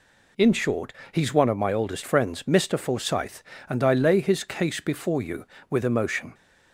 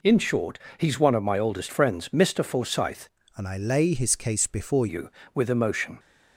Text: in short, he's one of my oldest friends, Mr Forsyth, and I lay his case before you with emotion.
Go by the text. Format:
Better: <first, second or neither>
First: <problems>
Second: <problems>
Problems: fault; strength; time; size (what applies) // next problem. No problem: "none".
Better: first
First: none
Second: changes voice from "and" to "before"; from 3.3 to 4.8 s; 1.5 s long